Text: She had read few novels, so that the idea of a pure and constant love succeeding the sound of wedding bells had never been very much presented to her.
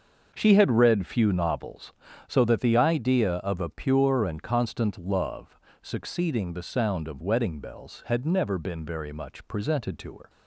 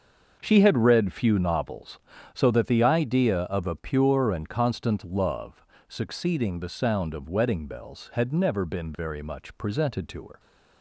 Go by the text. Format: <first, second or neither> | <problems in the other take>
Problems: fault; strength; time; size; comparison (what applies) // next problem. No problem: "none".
neither | starts louder than the rest; the same in both // pauses between "love" and "succeeding"; slight; the same in both